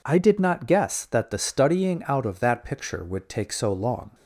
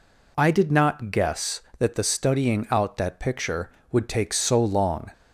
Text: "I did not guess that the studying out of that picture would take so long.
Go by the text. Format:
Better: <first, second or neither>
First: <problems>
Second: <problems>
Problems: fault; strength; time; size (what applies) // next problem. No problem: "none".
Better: first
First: none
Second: skips "of"; at 2.9 s